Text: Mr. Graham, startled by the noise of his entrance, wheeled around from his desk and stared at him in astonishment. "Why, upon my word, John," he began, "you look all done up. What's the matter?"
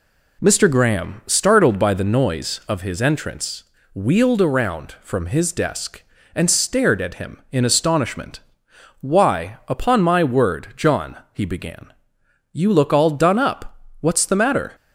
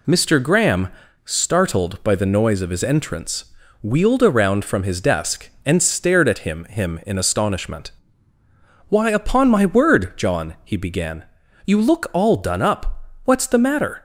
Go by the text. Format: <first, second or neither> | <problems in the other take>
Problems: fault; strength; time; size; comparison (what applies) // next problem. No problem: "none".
first | says "him" twice; at 6.6 s